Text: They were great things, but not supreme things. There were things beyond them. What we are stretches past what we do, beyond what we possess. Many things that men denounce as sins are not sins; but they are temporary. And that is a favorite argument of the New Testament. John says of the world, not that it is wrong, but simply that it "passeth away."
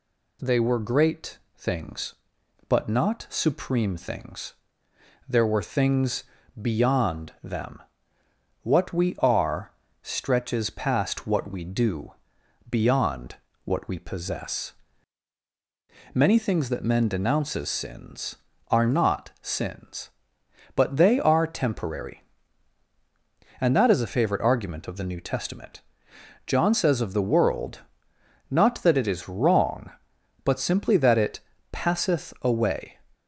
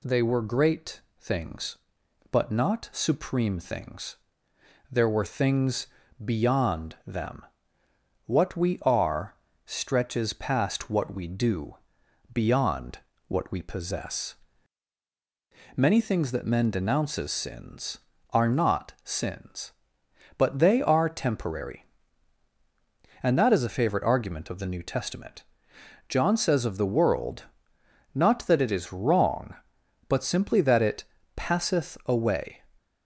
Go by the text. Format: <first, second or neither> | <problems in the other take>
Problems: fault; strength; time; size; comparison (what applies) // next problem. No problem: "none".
neither | pauses between "great" and "things"; slight; the same in both // pauses between "things" and "beyond"; slight; the same in both // pauses between "are" and "stretches"; slight; the same in both // pauses between "beyond" and "what"; slight; the same in both // pauses between "it" and "passeth"; slight; the same in both